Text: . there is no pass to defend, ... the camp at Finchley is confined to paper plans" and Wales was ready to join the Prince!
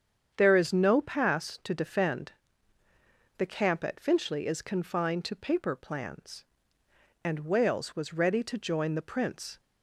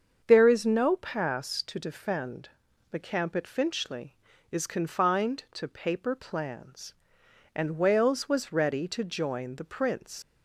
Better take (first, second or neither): first